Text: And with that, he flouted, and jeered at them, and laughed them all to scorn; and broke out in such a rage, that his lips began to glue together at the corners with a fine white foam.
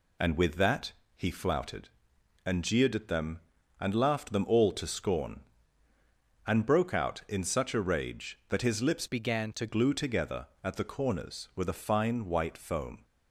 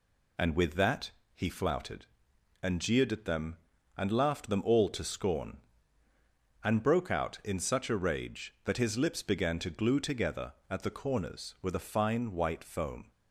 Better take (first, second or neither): second